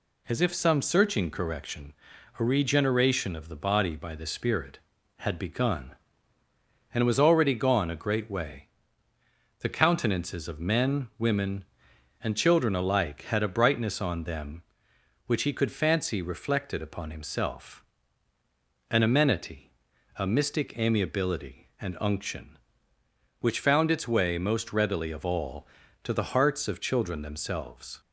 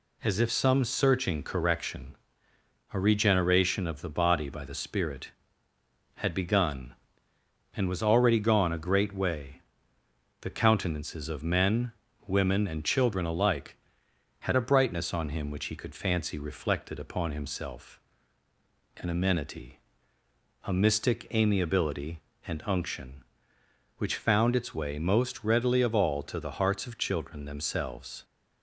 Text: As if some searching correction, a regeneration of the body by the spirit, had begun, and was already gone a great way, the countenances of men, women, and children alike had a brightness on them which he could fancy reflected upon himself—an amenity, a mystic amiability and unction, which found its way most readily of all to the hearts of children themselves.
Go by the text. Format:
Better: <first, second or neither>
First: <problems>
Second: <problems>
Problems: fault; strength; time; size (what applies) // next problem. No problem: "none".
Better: first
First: none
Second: says "him" for "them"; at 15.2 s